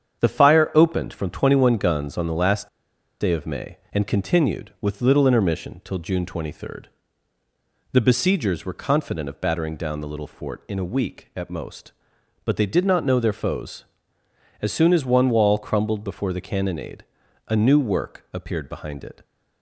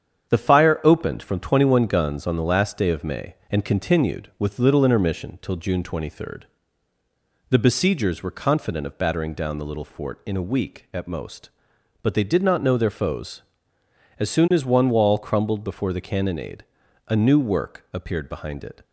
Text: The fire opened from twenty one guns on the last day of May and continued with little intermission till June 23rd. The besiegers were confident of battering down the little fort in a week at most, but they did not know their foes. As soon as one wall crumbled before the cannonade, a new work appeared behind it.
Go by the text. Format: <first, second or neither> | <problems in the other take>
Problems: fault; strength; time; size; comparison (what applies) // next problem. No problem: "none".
second | starts louder than the rest; strong; until 1.2 s; 8 dB; strong in the second // pauses between "last" and "day"; noticeable; at 2.6 s; 0.53 s long